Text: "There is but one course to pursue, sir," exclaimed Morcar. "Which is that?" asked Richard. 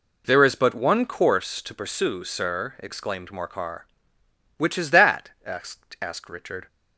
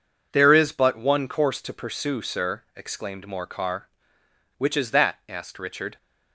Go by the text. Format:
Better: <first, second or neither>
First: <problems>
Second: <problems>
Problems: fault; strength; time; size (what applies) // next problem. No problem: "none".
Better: second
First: says "asked" twice; at 5.9 s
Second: none